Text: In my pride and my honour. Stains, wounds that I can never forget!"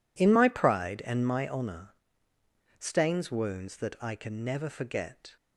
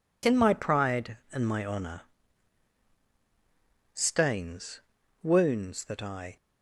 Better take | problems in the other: first | stops before "can never forget"; at 6.3 s

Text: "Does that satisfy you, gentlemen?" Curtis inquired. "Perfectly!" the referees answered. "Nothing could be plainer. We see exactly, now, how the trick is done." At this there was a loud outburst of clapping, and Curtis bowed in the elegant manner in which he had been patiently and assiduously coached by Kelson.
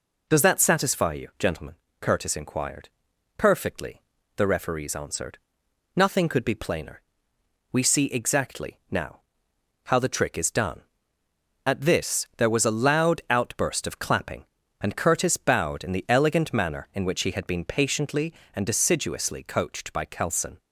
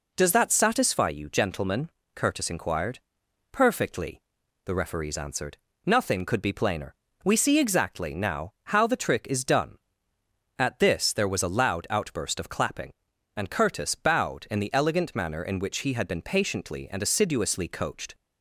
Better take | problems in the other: first | stops before "by Kelson"; at 18.1 s

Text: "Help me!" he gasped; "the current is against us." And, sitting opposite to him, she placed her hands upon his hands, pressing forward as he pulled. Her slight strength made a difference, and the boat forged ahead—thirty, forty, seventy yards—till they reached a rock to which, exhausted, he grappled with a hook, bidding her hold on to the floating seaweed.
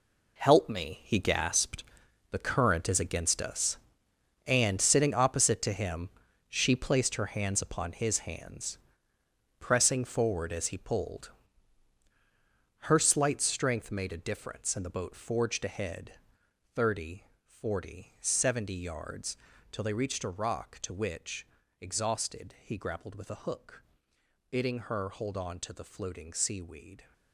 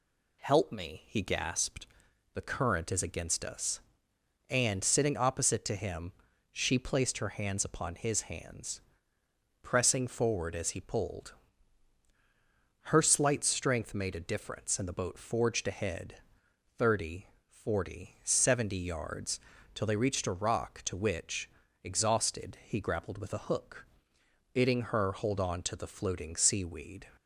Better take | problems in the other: second | gets quieter; strong; throughout; 11.5 dB

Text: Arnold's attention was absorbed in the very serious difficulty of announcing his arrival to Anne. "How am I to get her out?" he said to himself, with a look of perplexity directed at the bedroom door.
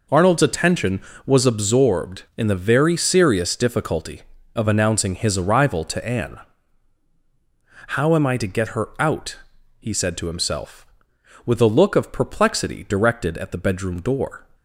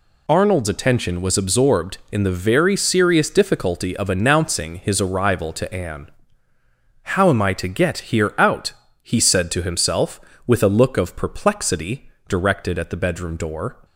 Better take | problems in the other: first | says "here" for "her"; at 8.0 s // pauses between "perplexity" and "directed"; slight; at 12.0 s; 0.18 s long

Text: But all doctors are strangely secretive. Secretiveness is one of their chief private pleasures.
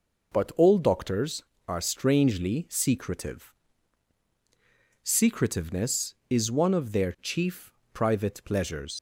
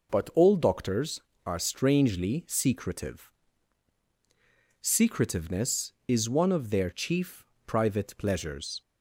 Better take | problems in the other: second | pauses between "chief" and "private"; slight; at 7.7 s; 0.22 s long; slight in the second // leaves "pleasures" unfinished; at 8.9 s; 90 ms

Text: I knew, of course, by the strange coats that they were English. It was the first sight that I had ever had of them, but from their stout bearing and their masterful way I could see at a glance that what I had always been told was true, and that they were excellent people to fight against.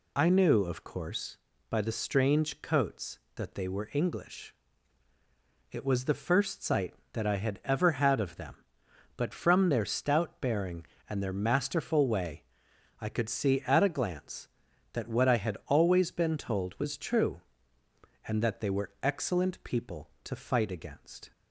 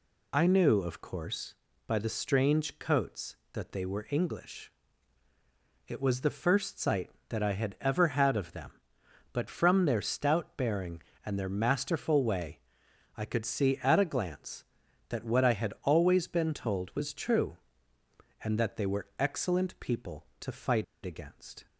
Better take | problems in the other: first | pauses between "way" and "I"; noticeable; at 12.5 s; 0.56 s long; noticeable in the first // pauses between "fight" and "against"; slight; at 20.8 s; 0.20 s long

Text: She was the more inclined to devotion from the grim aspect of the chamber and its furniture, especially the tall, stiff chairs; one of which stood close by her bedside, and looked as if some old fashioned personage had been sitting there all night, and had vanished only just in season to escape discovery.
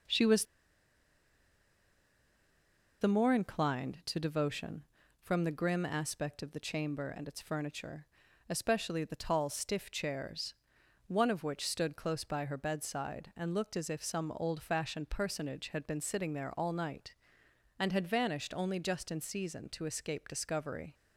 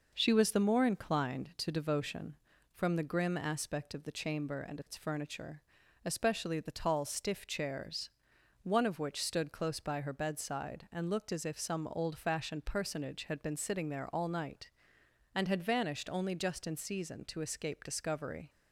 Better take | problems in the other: second | pauses between "was" and "the"; strong; at 0.4 s; 2.5 s long

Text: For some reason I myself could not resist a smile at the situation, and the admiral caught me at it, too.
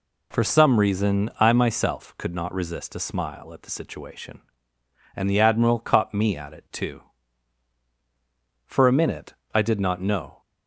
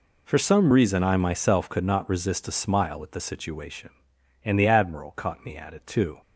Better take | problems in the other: second | goes on to say "For a minute I did not know"; strong; from 8.6 s on; 1.7 s long

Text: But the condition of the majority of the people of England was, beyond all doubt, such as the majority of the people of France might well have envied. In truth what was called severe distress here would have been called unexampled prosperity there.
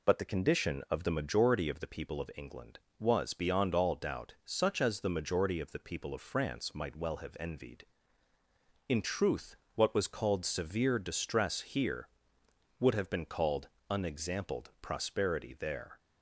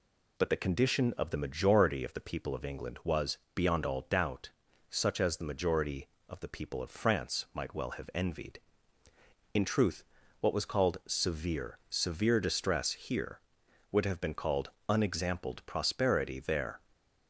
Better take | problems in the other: first | pauses between "truth" and "what"; slight; at 10.0 s; 0.36 s long; slight in the first // says "severe" twice; at 11.8 s // pauses between "called" and "unexampled"; slight; at 14.6 s; 0.18 s long; slight in the first // stays silent after the last word; slight; from 16.7 s on; 0.5 s long

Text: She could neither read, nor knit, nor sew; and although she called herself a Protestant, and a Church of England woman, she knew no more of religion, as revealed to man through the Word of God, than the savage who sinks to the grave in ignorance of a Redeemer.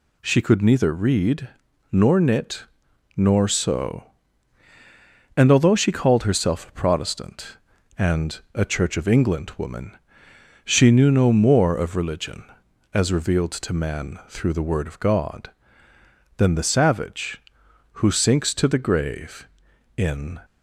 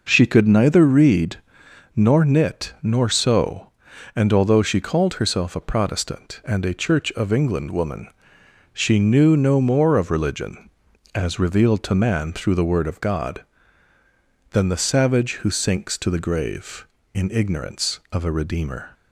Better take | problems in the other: second | stops before "ignorance of a Redeemer"; at 20.4 s

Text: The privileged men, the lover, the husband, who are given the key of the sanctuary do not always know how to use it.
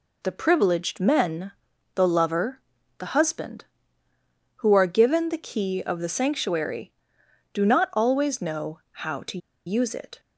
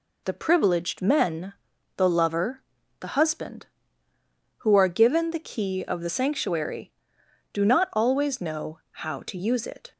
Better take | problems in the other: second | pauses between "to" and "use"; slight; at 9.3 s; 0.28 s long

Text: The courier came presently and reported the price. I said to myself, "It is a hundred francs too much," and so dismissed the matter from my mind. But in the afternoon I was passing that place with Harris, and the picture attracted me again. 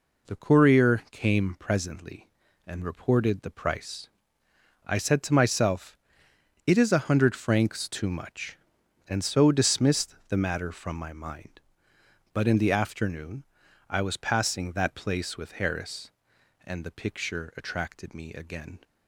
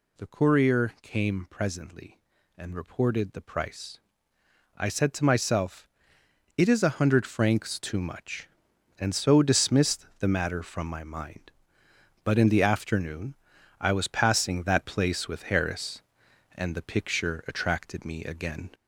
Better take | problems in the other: first | gets louder; slight; throughout; 2.5 dB // pauses between "afternoon" and "I"; at 13.3 s; 0.44 s long; also in the first

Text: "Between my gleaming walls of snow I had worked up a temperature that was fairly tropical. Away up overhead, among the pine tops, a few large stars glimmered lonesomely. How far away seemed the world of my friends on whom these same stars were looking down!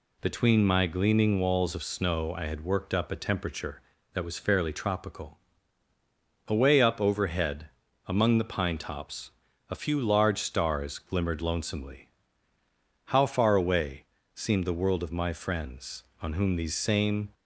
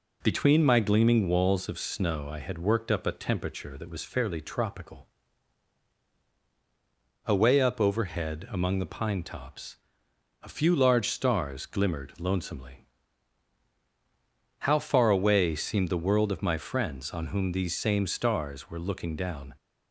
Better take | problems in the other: second | pauses between "away" and "seemed"; slight; at 14.0 s; 0.30 s long // stops before "stars were looking down"; at 17.3 s

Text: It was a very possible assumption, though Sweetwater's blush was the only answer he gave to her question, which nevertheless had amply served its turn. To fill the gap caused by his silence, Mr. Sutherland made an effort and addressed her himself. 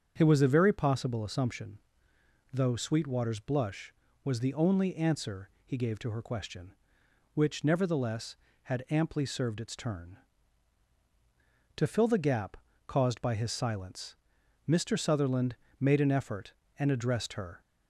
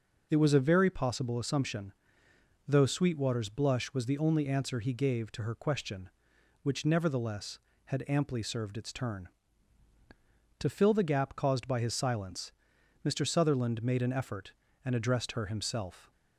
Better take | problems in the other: second | starts louder than the rest; strong; until 1.1 s; 7.5 dB // pauses between "gap" and "caused"; slight; at 12.5 s; 0.30 s long // pauses between "Sutherland" and "made"; slight; at 15.5 s; 0.24 s long // stops before "himself"; at 17.6 s

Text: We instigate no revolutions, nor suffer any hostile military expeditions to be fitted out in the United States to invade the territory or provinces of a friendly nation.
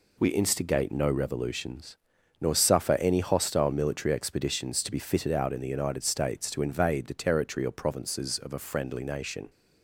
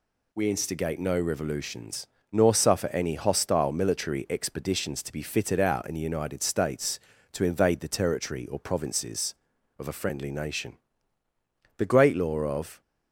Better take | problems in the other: first | goes on to say "The great law of"; noticeable; from 11.7 s on; 1.0 s long

